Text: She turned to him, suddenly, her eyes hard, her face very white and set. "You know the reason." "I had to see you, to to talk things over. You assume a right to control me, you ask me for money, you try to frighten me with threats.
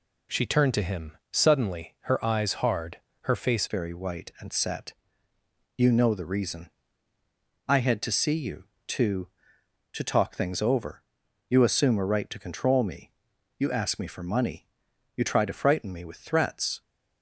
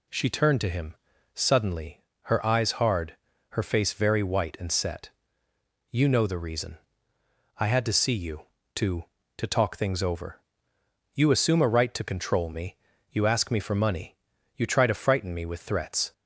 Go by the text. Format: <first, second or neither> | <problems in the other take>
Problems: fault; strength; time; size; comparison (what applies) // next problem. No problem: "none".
second | changes voice at "very"; from 3.6 s on; 13.2 s long